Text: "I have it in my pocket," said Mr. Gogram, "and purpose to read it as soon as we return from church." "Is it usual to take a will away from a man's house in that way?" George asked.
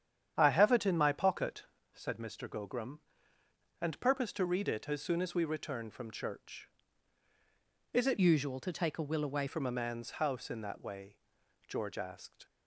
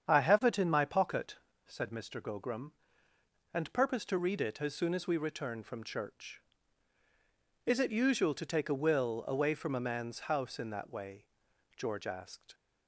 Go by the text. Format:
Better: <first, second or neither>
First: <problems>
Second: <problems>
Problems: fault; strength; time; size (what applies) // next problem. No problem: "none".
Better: second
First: starts louder than the rest; strong; until 1.3 s; 9 dB // changes voice from "usual" to "away"; from 8.1 to 9.4 s; 1.3 s long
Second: starts louder than the rest; strong; until 1.1 s; 8 dB